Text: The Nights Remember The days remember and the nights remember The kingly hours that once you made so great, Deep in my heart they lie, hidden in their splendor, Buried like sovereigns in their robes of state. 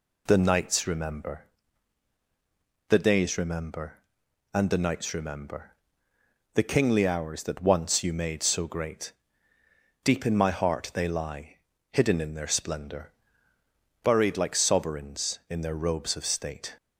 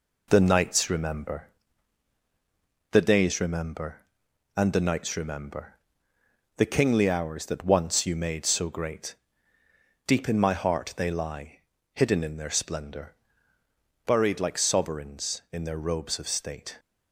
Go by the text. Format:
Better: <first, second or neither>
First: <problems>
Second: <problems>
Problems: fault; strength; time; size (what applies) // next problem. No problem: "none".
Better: first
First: pauses between "Remember" and "The"; strong; at 1.4 s; 1.4 s long // pauses between "remember" and "The"; noticeable; at 5.7 s; 0.82 s long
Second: gets quieter; noticeable; throughout; 4.5 dB // pauses between "Remember" and "The"; strong; at 1.4 s; 1.4 s long // pauses between "remember" and "The"; noticeable; at 5.7 s; 0.82 s long